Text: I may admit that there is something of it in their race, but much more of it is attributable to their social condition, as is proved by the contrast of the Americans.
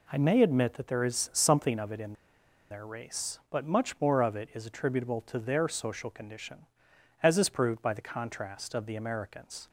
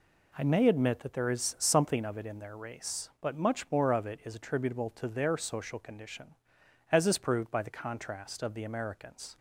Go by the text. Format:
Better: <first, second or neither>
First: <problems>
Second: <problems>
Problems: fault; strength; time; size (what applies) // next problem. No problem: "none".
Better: second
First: pauses between "in" and "their"; noticeable; at 2.1 s; 0.57 s long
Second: none